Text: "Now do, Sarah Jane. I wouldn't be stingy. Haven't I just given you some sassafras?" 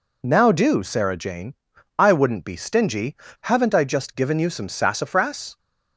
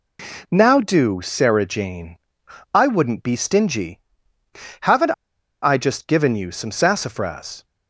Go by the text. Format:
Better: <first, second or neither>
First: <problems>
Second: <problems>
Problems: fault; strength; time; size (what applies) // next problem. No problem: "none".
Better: first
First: none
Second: pauses between "Haven't" and "I"; noticeable; at 5.1 s; 0.49 s long